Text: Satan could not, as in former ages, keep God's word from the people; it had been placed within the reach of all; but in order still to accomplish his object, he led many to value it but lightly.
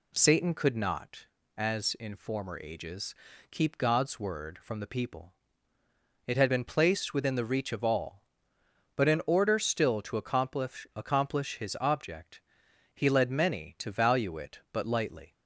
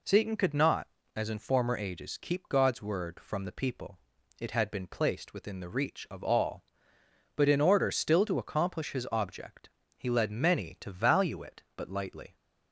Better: second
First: says "accomplish" twice; at 10.9 s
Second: none

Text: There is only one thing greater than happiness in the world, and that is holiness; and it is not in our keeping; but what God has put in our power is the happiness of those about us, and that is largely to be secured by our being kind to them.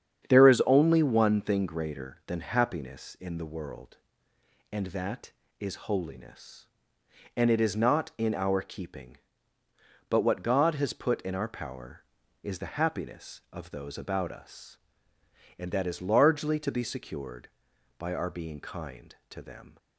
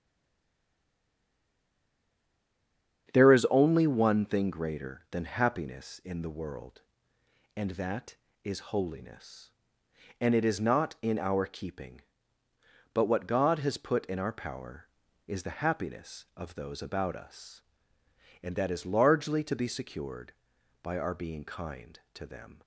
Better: first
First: starts louder than the rest; strong; until 1.3 s; 8.5 dB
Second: stays silent before the first word; strong; until 3.0 s; 3.0 s long // starts louder than the rest; strong; until 4.1 s; 8.5 dB

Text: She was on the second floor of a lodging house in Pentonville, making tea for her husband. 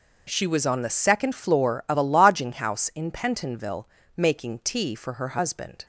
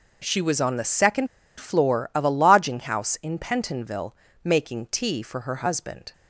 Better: first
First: none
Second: pauses between "second" and "floor"; slight; at 1.2 s; 0.32 s long

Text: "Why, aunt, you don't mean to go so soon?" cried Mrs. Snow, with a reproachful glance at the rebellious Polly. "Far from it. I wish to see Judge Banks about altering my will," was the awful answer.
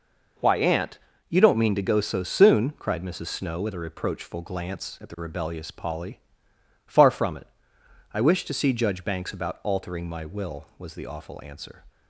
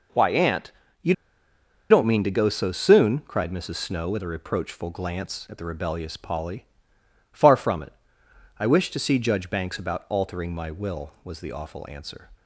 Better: first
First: none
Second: pauses between "you" and "don't"; noticeable; at 1.1 s; 0.76 s long

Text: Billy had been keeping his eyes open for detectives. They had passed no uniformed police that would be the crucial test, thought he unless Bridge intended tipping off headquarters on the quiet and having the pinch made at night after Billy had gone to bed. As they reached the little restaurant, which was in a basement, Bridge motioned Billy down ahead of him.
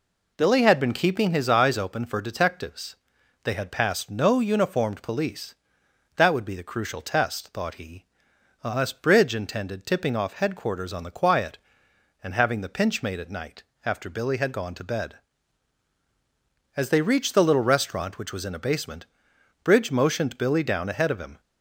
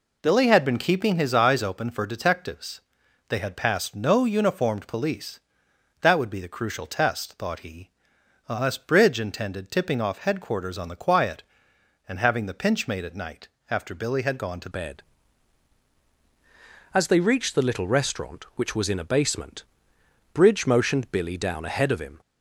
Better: first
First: pauses between "he" and "unless"; noticeable; at 8.0 s; 0.58 s long // pauses between "night" and "after"; slight; at 13.6 s; 0.22 s long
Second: pauses between "he" and "unless"; noticeable; at 7.8 s; 0.58 s long // pauses between "night" and "after"; slight; at 13.4 s; 0.22 s long // changes voice at "bed"; from 14.7 s on; 7.4 s long

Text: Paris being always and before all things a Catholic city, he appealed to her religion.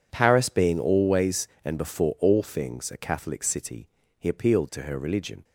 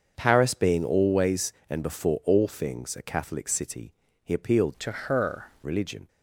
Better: first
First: none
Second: starts louder than the rest; until 1.1 s; 6.5 dB // changes voice from "to" to "her"; from 4.7 to 5.4 s; 0.7 s long

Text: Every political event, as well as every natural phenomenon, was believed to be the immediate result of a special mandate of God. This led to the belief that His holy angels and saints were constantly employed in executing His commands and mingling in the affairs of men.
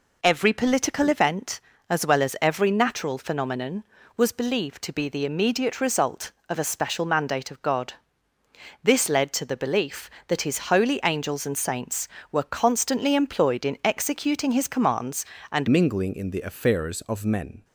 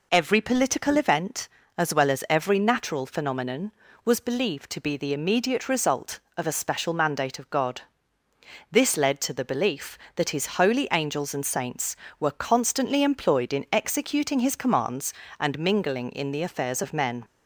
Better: second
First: changes voice at "mingling"; from 15.7 s on; 1.9 s long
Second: none

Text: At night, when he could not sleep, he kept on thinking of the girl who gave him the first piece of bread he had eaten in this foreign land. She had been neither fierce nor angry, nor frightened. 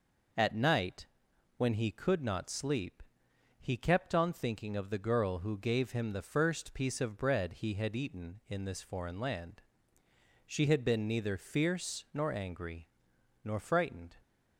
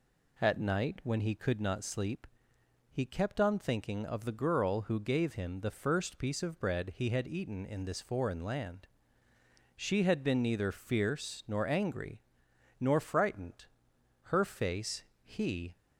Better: first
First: none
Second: goes on to say "Her face he"; from 14.2 s on; 1.5 s long

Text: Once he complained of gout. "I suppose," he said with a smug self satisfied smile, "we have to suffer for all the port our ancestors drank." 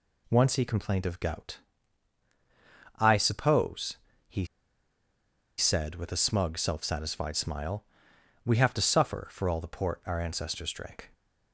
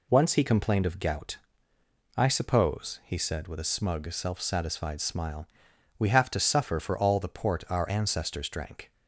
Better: second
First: pauses between "he" and "said"; at 4.4 s; 1.1 s long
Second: none

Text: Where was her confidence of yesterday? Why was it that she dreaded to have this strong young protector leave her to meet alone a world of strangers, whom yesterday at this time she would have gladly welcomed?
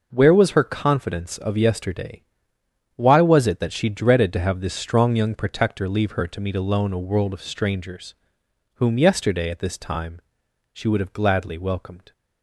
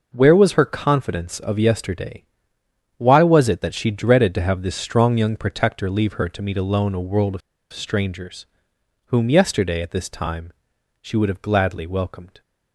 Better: first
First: pauses between "time" and "she"; noticeable; at 10.1 s; 0.52 s long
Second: pauses between "of" and "strangers"; slight; at 7.4 s; 0.32 s long // pauses between "time" and "she"; noticeable; at 10.5 s; 0.50 s long

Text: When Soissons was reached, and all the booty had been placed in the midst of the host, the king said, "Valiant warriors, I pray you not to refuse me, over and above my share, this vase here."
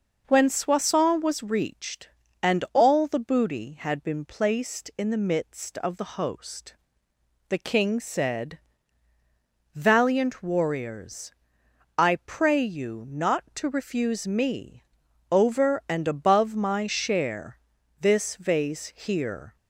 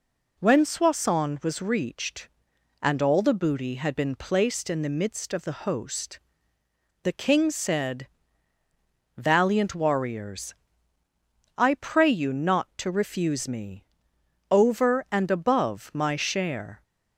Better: first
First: none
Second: stops before "this vase here"; at 16.8 s

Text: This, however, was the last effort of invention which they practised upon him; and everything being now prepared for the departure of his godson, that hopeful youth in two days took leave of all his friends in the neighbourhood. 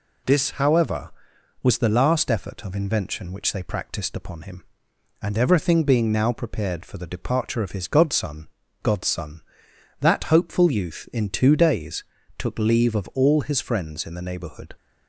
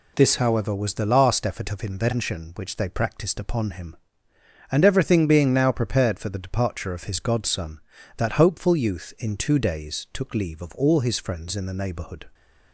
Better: second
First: says "godson" twice; at 8.8 s // pauses between "days" and "took"; slight; at 12.0 s; 0.34 s long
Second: none

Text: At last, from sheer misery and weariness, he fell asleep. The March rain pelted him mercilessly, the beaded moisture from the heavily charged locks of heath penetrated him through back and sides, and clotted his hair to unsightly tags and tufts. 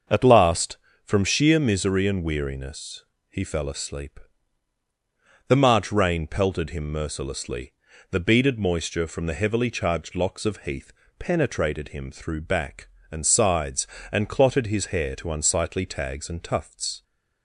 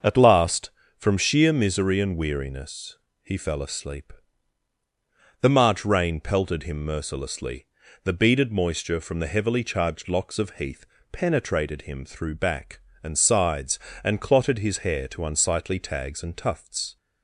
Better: neither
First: starts louder than the rest; until 1.3 s; 6.5 dB // pauses between "heath" and "penetrated"; slight; at 10.9 s; 0.26 s long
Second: starts louder than the rest; until 1.2 s; 6.5 dB // pauses between "heath" and "penetrated"; slight; at 10.8 s; 0.26 s long

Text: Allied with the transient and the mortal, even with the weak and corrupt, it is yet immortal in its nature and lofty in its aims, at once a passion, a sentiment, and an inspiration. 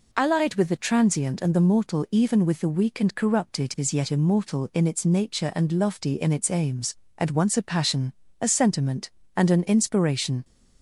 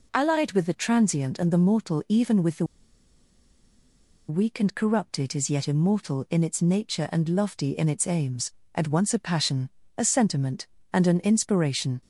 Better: first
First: none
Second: pauses between "the" and "weak"; strong; at 2.6 s; 1.6 s long

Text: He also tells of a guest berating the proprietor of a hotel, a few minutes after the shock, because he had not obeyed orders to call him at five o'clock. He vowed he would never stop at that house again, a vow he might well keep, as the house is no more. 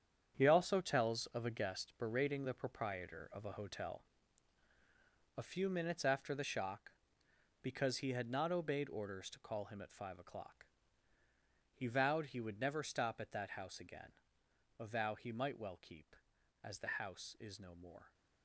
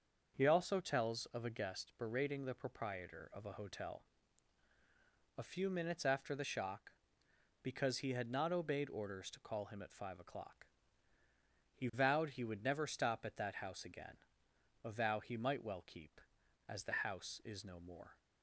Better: second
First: gets quieter; strong; throughout; 9.5 dB // starts louder than the rest; strong; until 1.3 s; 8.5 dB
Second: starts louder than the rest; until 1.3 s; 6.5 dB

